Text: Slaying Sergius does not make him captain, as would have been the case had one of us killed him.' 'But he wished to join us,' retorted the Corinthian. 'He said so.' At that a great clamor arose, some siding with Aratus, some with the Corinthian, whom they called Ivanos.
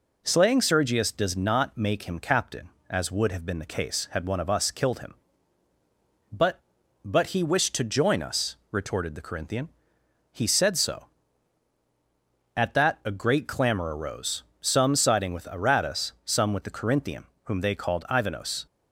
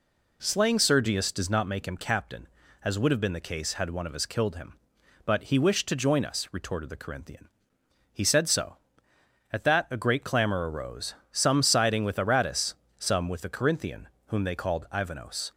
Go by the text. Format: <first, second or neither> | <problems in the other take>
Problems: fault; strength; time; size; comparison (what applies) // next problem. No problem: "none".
second | says "But" twice; at 7.0 s